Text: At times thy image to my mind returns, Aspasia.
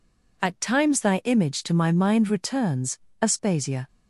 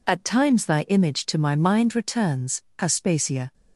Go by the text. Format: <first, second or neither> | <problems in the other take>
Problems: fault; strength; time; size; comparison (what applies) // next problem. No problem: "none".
neither | none